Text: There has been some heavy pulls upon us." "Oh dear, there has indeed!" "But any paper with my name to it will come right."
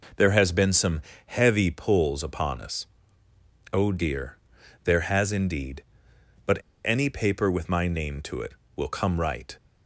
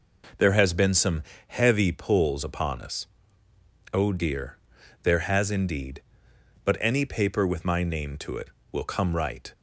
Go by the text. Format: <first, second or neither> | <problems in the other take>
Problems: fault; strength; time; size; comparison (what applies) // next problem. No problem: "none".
second | pauses between "some" and "heavy"; slight; at 1.0 s; 0.26 s long; slight in the second // pauses between "But" and "any"; slight; at 6.5 s; 0.27 s long